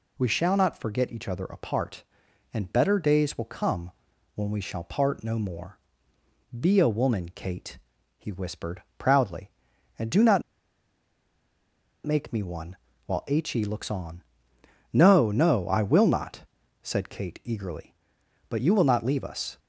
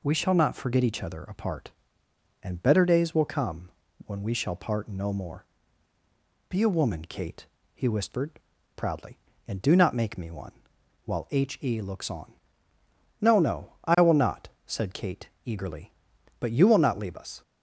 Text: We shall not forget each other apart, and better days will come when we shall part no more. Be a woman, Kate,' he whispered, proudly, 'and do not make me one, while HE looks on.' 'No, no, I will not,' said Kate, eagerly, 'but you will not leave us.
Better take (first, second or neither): second